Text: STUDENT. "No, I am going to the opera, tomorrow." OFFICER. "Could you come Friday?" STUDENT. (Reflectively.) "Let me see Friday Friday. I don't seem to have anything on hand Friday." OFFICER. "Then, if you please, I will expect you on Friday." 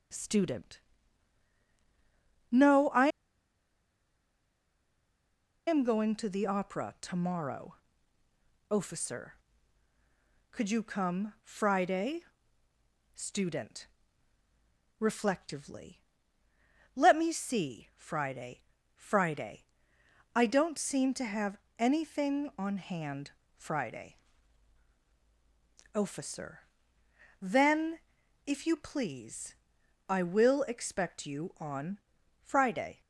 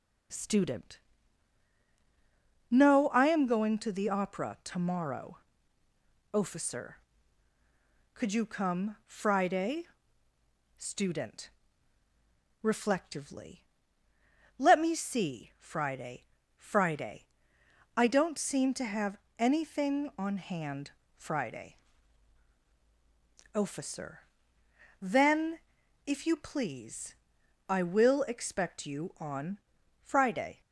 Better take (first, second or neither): second